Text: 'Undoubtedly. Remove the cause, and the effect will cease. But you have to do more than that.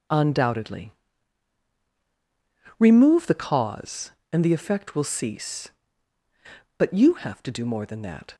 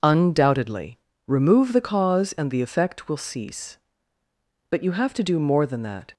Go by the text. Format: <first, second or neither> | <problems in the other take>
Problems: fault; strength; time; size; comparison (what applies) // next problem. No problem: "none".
neither | none